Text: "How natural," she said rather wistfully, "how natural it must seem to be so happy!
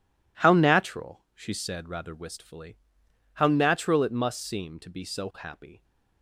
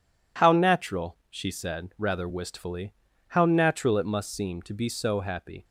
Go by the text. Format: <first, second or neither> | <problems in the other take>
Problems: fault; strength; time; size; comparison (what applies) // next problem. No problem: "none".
neither | none